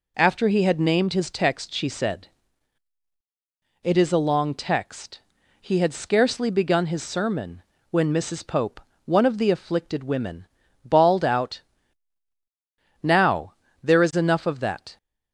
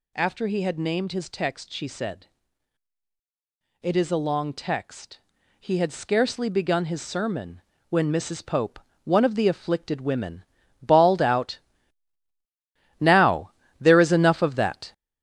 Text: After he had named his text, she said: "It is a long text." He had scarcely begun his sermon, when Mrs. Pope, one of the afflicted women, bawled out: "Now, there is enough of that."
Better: first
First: none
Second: gets louder; noticeable; throughout; 6 dB

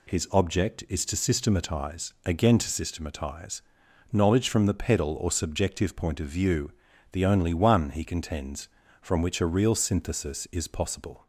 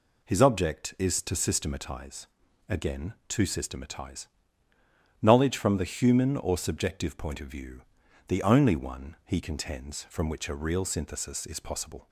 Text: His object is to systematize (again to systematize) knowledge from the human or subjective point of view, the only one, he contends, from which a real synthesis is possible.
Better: second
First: says "pedal" for "human"; at 4.7 s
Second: none

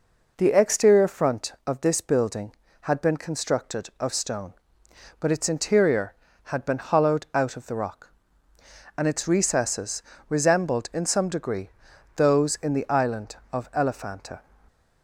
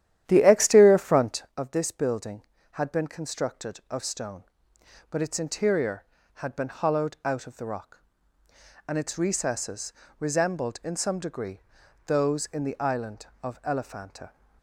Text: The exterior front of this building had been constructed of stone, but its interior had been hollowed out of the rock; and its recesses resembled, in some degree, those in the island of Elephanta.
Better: first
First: pauses between "recesses" and "resembled"; slight; at 10.0 s; 0.26 s long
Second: starts louder than the rest; strong; until 1.6 s; 11.5 dB // pauses between "recesses" and "resembled"; slight; at 9.9 s; 0.26 s long

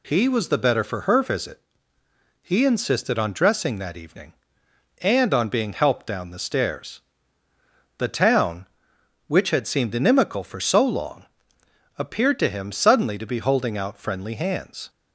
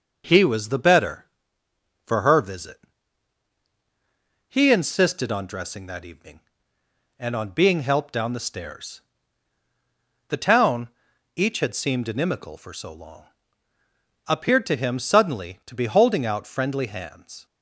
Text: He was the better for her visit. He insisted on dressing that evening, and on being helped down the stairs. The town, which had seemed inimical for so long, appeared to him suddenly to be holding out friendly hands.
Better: first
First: none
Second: says "each" for "which"; at 11.3 s

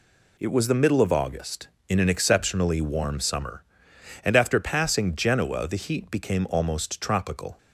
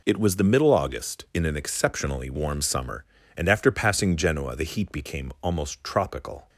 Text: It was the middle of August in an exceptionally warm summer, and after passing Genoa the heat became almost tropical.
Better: first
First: none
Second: skips "of"; at 0.7 s

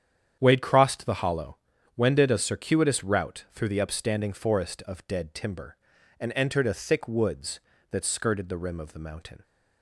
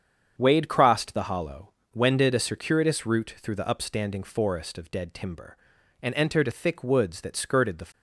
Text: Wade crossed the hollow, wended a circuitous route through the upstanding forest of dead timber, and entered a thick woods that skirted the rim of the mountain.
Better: first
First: starts louder than the rest; strong; until 1.4 s; 9 dB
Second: starts louder than the rest; strong; until 1.3 s; 7.5 dB // stops before "rim of the mountain"; at 7.9 s

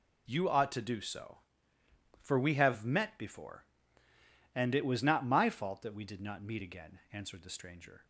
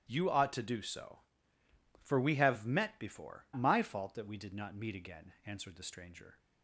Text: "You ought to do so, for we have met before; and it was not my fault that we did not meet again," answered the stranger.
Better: first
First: none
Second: starts louder than the rest; strong; until 1.0 s; 13 dB // skips "and it was not"; at 3.5 s

